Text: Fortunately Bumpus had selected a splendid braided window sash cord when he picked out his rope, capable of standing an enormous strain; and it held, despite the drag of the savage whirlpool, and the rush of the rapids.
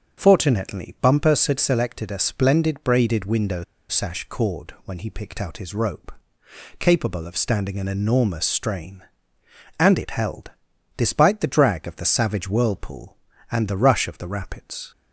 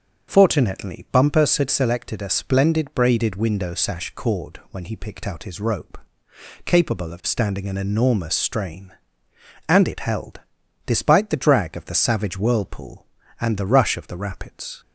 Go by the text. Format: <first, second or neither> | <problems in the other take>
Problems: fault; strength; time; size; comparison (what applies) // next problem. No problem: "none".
second | starts louder than the rest; noticeable; until 1.2 s; 6 dB; also in the second // pauses between "window" and "sash"; slight; at 3.6 s; 0.26 s long